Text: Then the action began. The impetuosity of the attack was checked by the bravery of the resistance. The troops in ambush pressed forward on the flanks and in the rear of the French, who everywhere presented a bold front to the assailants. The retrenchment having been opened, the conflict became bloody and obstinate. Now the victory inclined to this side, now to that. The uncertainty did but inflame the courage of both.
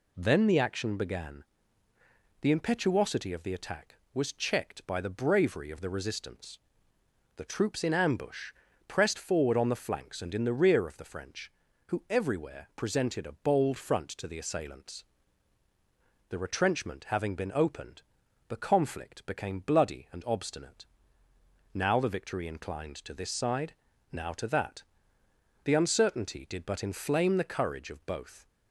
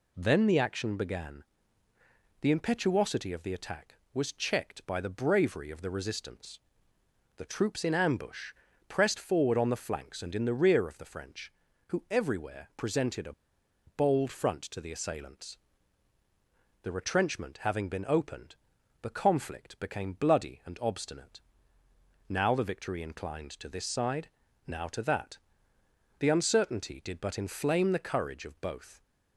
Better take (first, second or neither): first